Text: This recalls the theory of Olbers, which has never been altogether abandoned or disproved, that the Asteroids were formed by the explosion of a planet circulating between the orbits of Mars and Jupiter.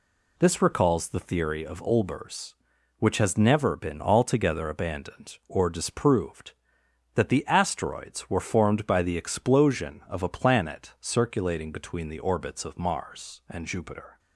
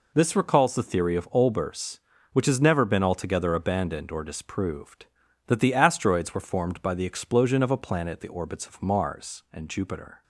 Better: first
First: none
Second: skips "circulating between"; at 8.2 s

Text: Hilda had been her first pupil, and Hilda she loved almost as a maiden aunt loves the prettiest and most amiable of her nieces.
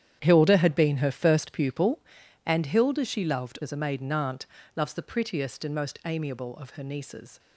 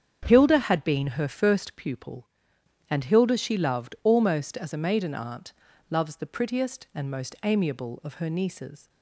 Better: second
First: starts louder than the rest; strong; until 1.2 s; 10 dB // skips "almost"; at 3.5 s // pauses between "aunt" and "loves"; slight; at 4.4 s; 0.28 s long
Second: starts louder than the rest; strong; until 1.2 s; 7.5 dB // pauses between "aunt" and "loves"; at 5.5 s; 0.38 s long

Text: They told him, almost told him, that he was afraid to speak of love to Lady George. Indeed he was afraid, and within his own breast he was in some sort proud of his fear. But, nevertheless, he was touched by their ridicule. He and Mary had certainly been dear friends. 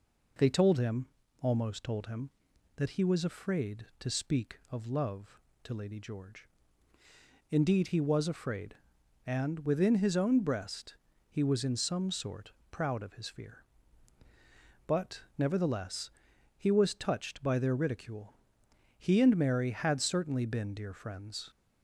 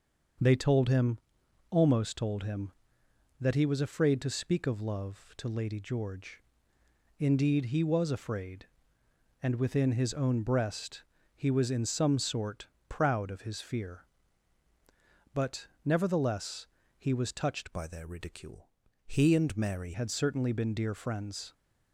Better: first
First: pauses between "breast" and "he"; slight; at 10.9 s; 0.36 s long // pauses between "sort" and "proud"; slight; at 12.5 s; 0.18 s long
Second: starts louder than the rest; until 1.9 s; 6.5 dB // pauses between "breast" and "he"; slight; at 11.0 s; 0.32 s long // pauses between "sort" and "proud"; slight; at 12.6 s; 0.20 s long // changes voice from "by" to "Mary"; from 17.7 to 19.9 s; 2.2 s long

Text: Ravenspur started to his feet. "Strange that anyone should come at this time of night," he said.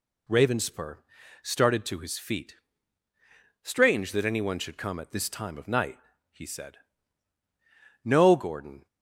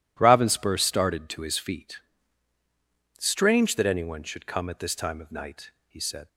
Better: second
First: pauses between "Ravenspur" and "started"; at 0.9 s; 0.44 s long // goes on to say "No Gordon"; noticeable; from 8.0 s on; 0.84 s long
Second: none

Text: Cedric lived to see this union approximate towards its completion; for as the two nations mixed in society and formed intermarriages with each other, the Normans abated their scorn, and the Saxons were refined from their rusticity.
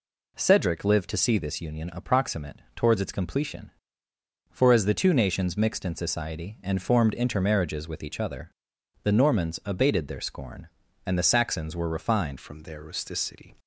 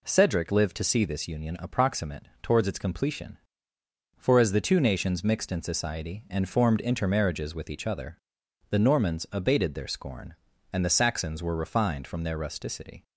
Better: second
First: changes voice at "from"; from 12.3 s on; 1.2 s long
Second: none

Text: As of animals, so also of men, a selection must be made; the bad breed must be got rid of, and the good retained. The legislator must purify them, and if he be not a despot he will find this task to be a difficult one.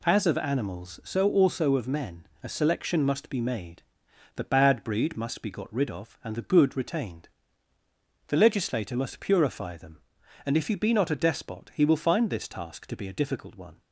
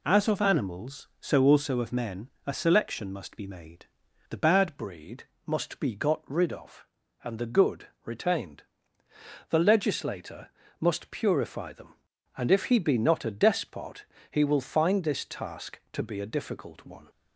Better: first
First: none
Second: changes voice at "breed"; from 4.7 s on; 12.3 s long // pauses between "breed" and "must"; slight; at 5.2 s; 0.24 s long // pauses between "good" and "retained"; slight; at 7.8 s; 0.16 s long // pauses between "legislator" and "must"; slight; at 10.4 s; 0.32 s long // pauses between "despot" and "he"; slight; at 14.0 s; 0.24 s long

